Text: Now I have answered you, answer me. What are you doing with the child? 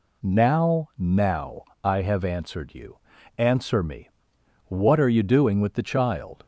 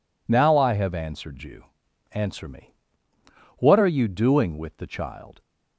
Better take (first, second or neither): second